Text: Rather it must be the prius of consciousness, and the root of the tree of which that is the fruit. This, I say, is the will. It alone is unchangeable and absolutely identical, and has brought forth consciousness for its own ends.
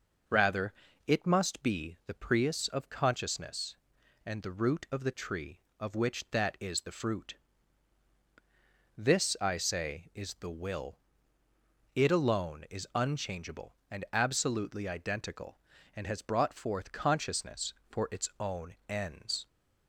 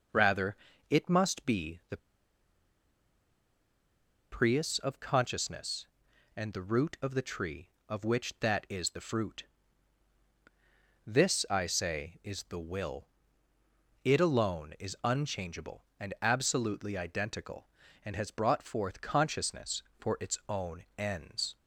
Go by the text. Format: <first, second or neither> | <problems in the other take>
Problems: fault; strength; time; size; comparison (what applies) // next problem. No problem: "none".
first | pauses between "Rather" and "it"; slight; at 0.5 s; 0.34 s long; slight in the first // pauses between "the" and "prius"; strong; at 1.9 s; 2.3 s long // pauses between "own" and "ends"; slight; at 20.8 s; 0.16 s long; slight in the first